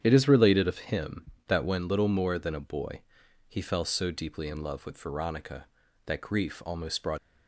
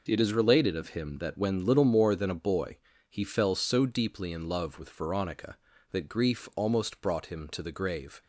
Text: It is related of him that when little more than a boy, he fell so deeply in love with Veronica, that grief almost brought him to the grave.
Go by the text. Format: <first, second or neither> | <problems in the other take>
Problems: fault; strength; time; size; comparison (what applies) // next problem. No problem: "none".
second | starts louder than the rest; strong; until 1.0 s; 9 dB // stops before "him to the grave"; at 7.1 s